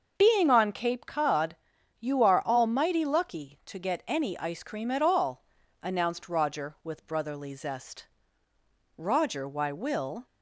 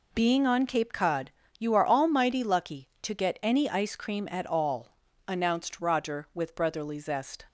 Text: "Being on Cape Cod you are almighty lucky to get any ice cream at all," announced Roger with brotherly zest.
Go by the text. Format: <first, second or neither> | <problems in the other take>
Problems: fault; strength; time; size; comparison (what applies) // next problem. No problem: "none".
second | starts louder than the rest; noticeable; until 1.1 s; 6 dB // pauses between "Cod" and "you"; at 1.5 s; 0.42 s long; slight in the second // goes on to say "Roger why will"; noticeable; from 8.9 s on; 1.3 s long